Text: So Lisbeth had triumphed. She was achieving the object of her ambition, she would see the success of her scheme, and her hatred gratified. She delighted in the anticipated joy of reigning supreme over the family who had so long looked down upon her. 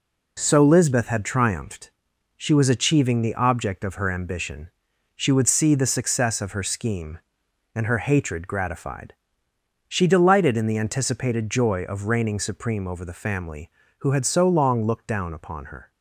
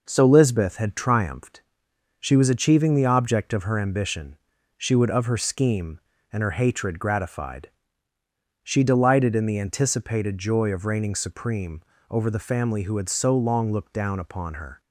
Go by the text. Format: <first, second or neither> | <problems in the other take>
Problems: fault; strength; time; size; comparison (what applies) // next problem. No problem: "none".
first | skips "see the success"; at 5.0 s // pauses between "supreme" and "over"; slight; at 11.8 s; 0.26 s long